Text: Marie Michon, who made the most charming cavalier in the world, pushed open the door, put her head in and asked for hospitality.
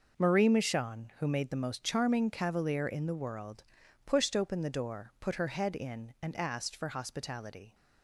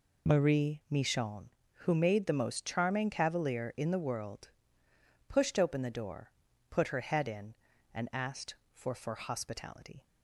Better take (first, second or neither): first